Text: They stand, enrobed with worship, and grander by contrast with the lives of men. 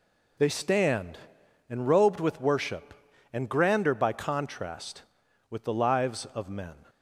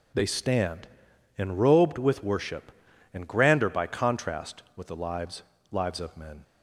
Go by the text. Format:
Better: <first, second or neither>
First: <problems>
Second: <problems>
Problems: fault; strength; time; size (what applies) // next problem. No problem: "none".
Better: first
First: none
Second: says "lives" twice; at 5.7 s